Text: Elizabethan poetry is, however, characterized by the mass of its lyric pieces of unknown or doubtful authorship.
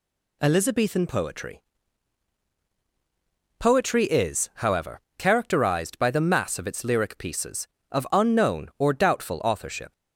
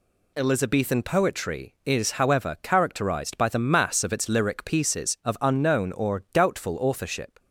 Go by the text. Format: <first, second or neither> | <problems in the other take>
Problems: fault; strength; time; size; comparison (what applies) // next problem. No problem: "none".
second | says "poetry" twice; at 3.5 s